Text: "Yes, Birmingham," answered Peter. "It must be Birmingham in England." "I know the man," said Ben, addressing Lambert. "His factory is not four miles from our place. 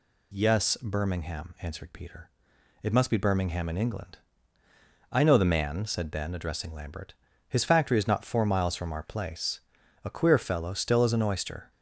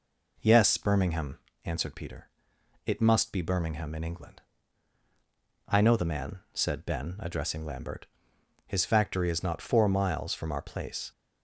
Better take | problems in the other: second | goes on to say "A queer fellow still as an oyster"; strong; from 10.0 s on; 1.6 s long

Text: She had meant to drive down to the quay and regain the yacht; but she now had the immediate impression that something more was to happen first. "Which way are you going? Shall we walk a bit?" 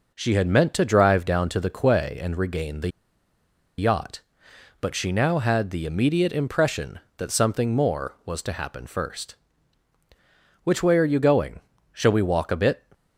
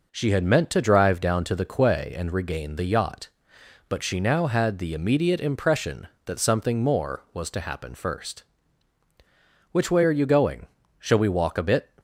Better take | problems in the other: second | pauses between "the" and "yacht"; noticeable; at 2.8 s; 0.89 s long

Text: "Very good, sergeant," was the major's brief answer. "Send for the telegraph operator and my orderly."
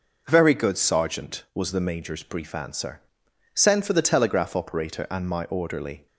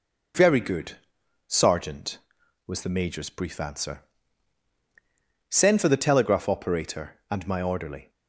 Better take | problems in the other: neither | none

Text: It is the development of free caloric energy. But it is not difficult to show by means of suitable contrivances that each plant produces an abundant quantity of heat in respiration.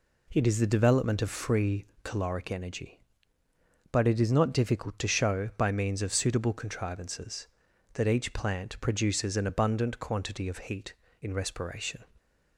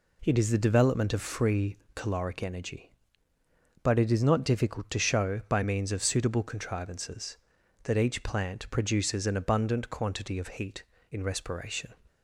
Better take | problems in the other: neither | pauses between "free" and "caloric"; slight; the same in both

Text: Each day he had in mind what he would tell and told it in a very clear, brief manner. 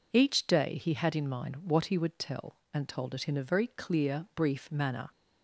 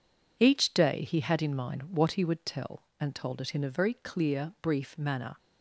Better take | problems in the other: first | gets quieter; strong; throughout; 8.5 dB

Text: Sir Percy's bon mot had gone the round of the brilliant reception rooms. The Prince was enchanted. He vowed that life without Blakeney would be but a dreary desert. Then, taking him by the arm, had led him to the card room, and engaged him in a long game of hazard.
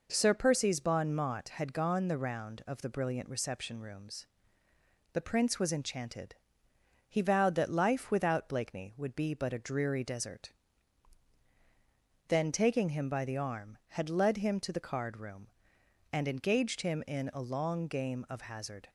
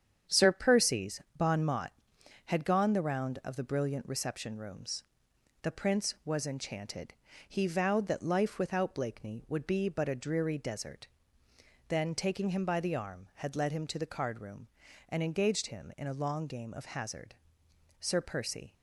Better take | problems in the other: first | starts louder than the rest; strong; until 1.4 s; 8.5 dB // pauses between "Percy's" and "bon"; slight; at 1.2 s; 0.16 s long // goes on to say "Sir Percy"; noticeable; from 18.0 s on; 0.72 s long

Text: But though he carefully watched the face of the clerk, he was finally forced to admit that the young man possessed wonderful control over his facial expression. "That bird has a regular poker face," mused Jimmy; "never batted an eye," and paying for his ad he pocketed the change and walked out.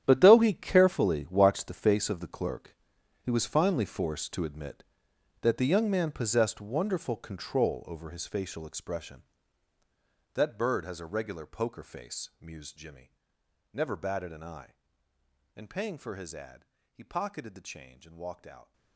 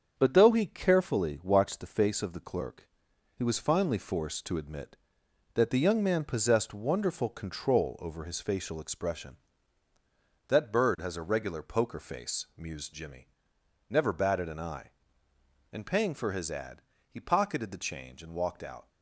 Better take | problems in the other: second | gets quieter; strong; throughout; 14.5 dB // starts louder than the rest; strong; until 1.0 s; 10.5 dB; strong in the second // pauses between "ad" and "he"; slight; at 16.6 s; 0.28 s long; slight in the second

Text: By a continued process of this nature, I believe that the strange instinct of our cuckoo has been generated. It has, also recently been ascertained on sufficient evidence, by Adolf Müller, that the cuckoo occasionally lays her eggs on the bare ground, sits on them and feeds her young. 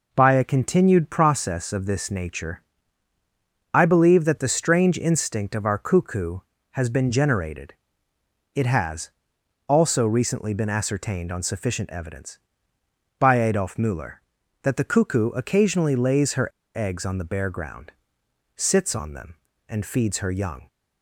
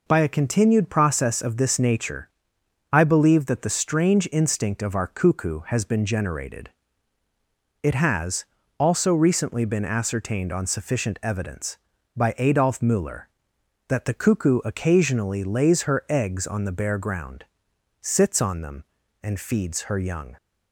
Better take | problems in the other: second | pauses between "her" and "eggs"; slight; at 16.4 s; 0.25 s long

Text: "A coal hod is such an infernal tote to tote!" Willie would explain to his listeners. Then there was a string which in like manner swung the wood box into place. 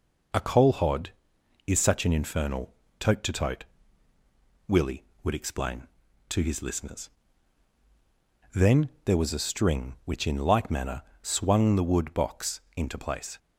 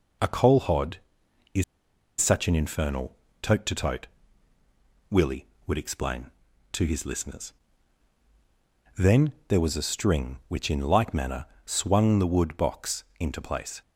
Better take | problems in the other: first | pauses between "is" and "such"; noticeable; at 1.6 s; 0.57 s long // pauses between "infernal" and "tote"; slight; at 3.1 s; 0.24 s long; slight in the first // pauses between "Then" and "there"; slight; at 9.3 s; 0.16 s long; slight in the first // pauses between "manner" and "swung"; slight; at 11.4 s; 0.20 s long; slight in the first // pauses between "box" and "into"; slight; at 13.0 s; 0.16 s long; slight in the first

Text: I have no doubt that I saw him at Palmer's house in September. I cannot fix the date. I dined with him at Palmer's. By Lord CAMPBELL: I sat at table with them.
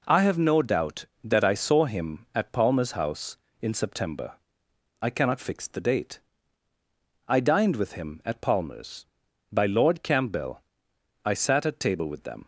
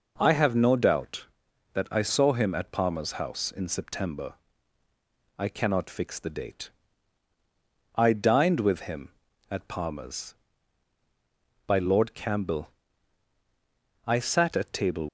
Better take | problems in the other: first | stops before "with them"; at 15.0 s

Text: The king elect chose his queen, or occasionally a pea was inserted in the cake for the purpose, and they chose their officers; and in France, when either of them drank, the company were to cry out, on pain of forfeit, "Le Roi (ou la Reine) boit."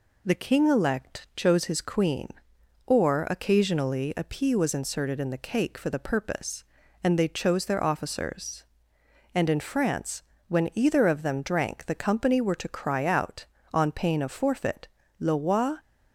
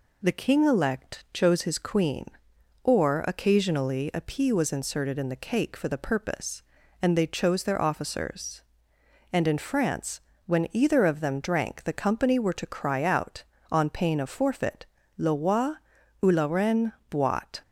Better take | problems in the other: second | stops before "ou la Reine boit"; at 15.7 s

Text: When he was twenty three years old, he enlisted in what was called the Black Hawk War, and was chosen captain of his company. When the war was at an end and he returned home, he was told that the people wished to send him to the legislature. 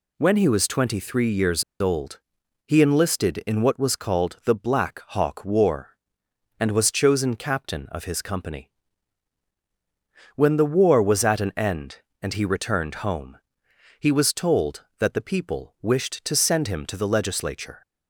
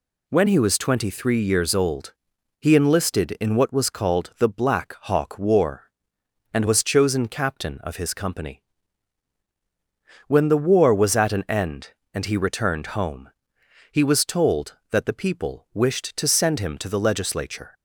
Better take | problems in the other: second | pauses between "years" and "old"; slight; at 1.6 s; 0.18 s long

